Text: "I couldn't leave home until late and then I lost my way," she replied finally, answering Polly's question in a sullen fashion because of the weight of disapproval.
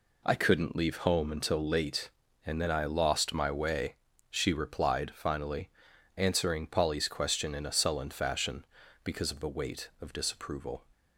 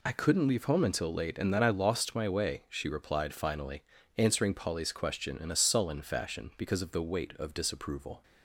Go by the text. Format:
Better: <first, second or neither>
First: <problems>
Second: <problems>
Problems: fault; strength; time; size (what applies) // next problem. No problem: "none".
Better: neither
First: none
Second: none